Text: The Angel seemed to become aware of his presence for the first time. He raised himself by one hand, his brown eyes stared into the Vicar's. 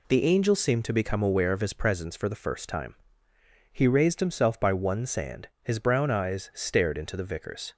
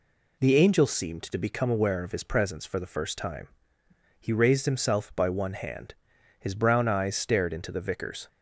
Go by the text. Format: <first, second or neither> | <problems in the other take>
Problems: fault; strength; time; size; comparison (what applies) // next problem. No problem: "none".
second | says "sand" for "hand"; at 5.0 s